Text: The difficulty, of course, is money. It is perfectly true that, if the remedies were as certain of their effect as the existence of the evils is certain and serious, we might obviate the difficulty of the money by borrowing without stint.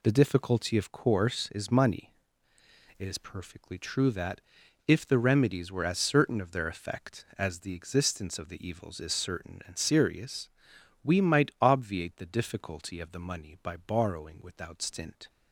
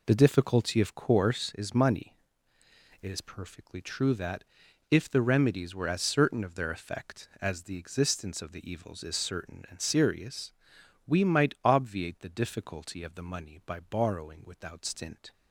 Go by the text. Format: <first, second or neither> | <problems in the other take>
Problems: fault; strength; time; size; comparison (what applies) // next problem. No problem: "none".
first | starts louder than the rest; until 1.3 s; 3.5 dB